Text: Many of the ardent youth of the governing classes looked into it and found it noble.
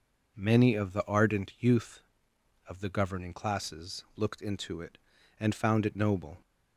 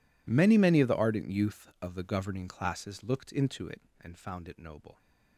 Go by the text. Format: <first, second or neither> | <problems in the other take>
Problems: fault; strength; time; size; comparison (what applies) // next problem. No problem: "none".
first | says "Many" twice; at 0.5 s